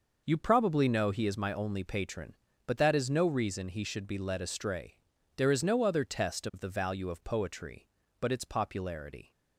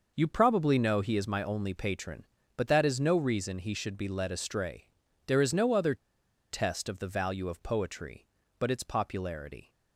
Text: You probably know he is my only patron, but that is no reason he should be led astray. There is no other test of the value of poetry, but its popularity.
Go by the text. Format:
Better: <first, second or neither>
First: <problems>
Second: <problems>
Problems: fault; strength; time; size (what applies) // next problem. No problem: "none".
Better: first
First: none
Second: pauses between "other" and "test"; noticeable; at 5.9 s; 0.55 s long